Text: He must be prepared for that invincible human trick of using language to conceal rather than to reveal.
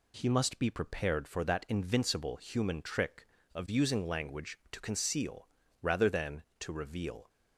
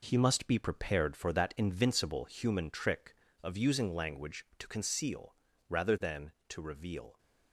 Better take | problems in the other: first | gets quieter; throughout; 7 dB // pauses between "conceal" and "rather"; slight; at 5.3 s; 0.36 s long; slight in the first

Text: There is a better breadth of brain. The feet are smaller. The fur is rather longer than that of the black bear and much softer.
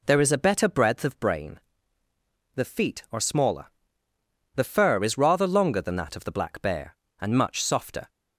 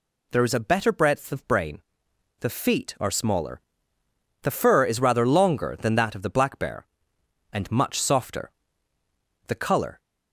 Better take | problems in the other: first | goes on to say "The color"; from 9.4 s on; 0.52 s long

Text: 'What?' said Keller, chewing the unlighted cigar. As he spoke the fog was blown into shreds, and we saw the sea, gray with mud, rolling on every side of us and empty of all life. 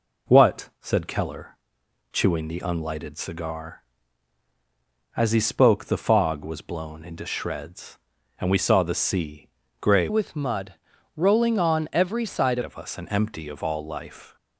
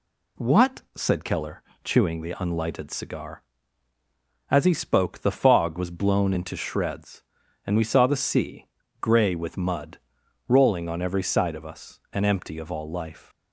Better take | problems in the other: second | changes voice from "with" to "side"; from 10.0 to 12.6 s; 2.6 s long

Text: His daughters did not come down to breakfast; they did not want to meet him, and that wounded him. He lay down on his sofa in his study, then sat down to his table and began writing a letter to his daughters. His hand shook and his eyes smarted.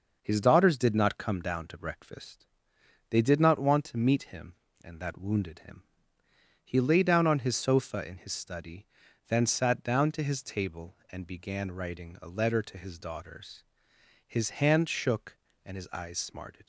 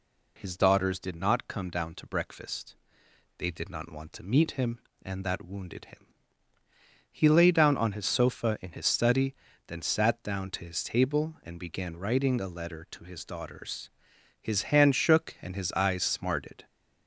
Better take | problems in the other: neither | none

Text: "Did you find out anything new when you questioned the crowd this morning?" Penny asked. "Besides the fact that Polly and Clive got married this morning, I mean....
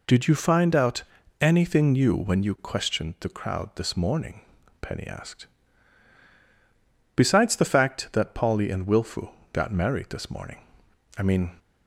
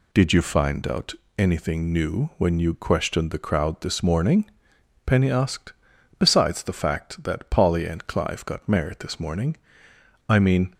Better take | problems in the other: second | pauses between "out" and "anything"; slight; at 1.0 s; 0.36 s long; slight in the second // says "Wilfu" for "Clive"; at 8.8 s

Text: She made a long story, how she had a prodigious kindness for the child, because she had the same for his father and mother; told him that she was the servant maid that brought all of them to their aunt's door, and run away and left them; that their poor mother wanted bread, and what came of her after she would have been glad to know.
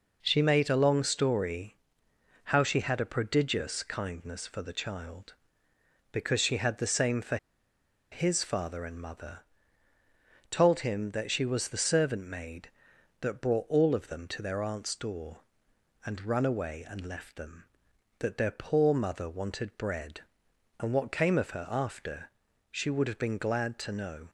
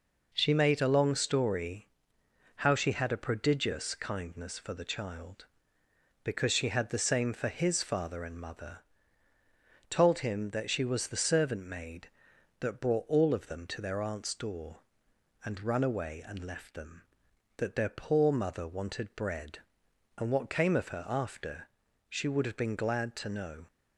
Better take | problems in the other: second | pauses between "for" and "his"; noticeable; at 7.3 s; 0.75 s long // pauses between "after" and "she"; at 22.2 s; 0.42 s long; also in the second

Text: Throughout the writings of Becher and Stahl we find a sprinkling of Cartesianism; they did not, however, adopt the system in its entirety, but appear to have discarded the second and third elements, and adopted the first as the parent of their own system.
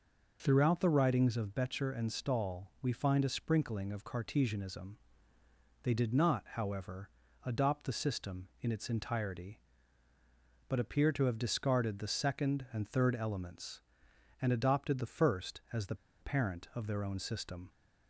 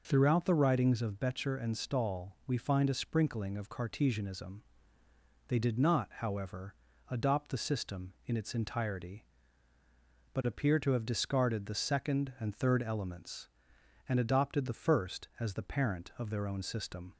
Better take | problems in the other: second | pauses between "the" and "parent"; slight; at 15.9 s; 0.26 s long

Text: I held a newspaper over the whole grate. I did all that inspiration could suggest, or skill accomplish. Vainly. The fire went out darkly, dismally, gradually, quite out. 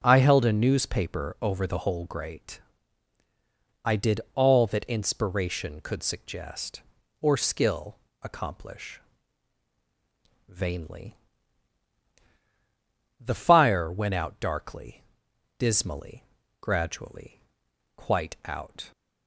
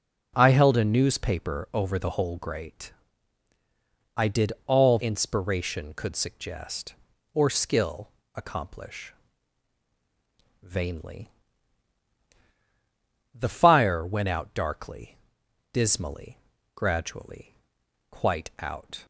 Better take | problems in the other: first | pauses between "did" and "all"; slight; at 4.5 s; 0.16 s long; slight in the first // skips "that"; at 4.9 s // pauses between "skill" and "accomplish"; slight; at 8.1 s; 0.22 s long; slight in the first

